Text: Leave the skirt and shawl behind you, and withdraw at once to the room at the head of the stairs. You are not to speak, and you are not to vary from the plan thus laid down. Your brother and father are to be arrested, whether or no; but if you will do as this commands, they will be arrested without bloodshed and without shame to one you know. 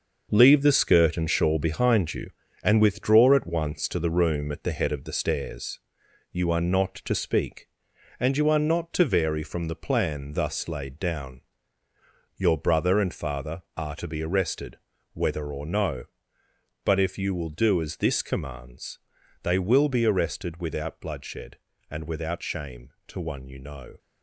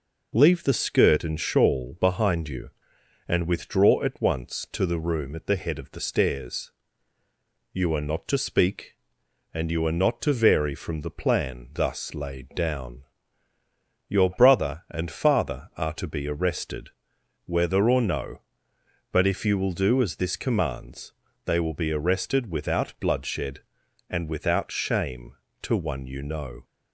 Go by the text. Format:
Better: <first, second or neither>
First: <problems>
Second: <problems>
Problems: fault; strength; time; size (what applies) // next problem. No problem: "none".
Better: second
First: gets quieter; strong; throughout; 8 dB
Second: none